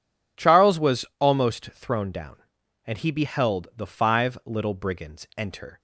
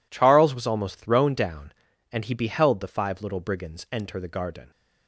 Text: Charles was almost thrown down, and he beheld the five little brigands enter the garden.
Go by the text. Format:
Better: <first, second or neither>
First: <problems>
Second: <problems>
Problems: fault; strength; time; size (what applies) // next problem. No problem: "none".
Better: second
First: pauses between "was" and "almost"; slight; at 1.0 s; 0.16 s long // stops before "the garden"; at 5.7 s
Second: none